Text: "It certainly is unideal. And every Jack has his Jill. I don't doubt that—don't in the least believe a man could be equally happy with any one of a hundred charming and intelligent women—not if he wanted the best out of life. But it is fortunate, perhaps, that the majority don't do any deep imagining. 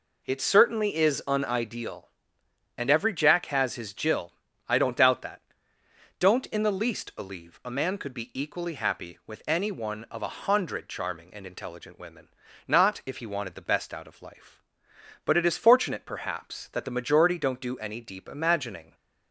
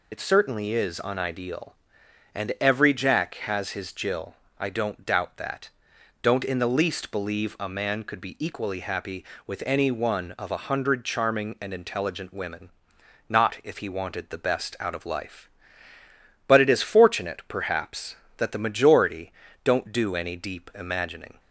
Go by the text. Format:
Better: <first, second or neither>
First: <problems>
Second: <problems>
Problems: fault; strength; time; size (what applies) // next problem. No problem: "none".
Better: first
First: none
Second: loses the start of "It"; at 0.1 s; 50 ms // pauses between "majority" and "don't"; slight; at 19.3 s; 0.30 s long